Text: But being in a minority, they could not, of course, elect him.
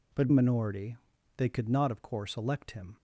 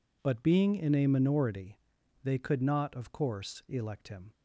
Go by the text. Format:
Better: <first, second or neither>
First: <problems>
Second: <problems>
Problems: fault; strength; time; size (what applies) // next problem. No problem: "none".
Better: second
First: skips "being in a"; at 0.3 s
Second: none